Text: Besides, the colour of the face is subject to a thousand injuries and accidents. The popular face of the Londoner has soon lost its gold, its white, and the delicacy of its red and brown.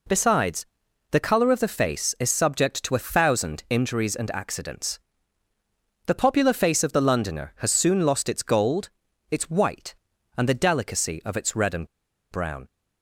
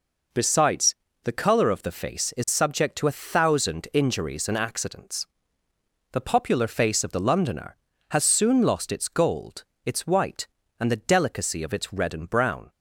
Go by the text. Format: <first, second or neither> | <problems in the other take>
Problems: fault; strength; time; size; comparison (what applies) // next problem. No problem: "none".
second | pauses between "and" and "brown"; at 11.8 s; 0.44 s long